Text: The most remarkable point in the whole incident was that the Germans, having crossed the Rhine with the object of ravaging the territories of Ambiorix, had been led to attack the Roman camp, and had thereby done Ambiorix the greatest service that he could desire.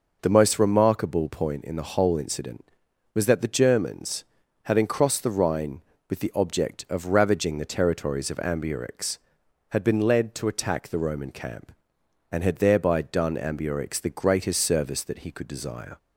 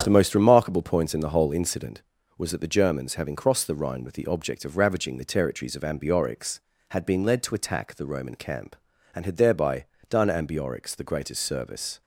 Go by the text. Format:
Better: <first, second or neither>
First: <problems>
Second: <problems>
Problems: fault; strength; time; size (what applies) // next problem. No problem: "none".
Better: first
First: none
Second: starts louder than the rest; strong; until 1.0 s; 8 dB // pauses between "thereby" and "done"; slight; at 9.8 s; 0.24 s long // stops before "that he could desire"; at 12.0 s